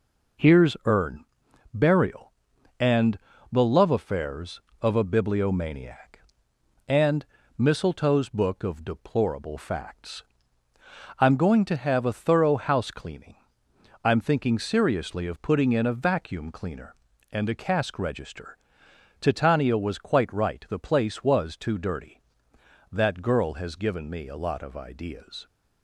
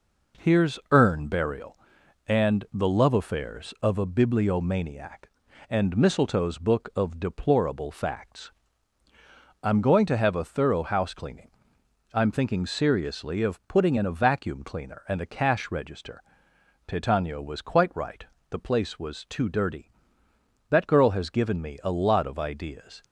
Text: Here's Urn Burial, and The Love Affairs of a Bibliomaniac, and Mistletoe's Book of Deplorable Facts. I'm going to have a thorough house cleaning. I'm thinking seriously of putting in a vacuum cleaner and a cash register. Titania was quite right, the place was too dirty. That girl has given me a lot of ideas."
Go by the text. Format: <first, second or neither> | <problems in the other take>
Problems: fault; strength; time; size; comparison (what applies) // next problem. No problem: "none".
second | pauses between "Urn" and "Burial"; noticeable; at 1.2 s; 0.48 s long // pauses between "and" and "The"; slight; at 3.1 s; 0.34 s long // pauses between "and" and "Mistletoe's"; slight; at 7.2 s; 0.32 s long // says "cask" for "cash"; at 17.5 s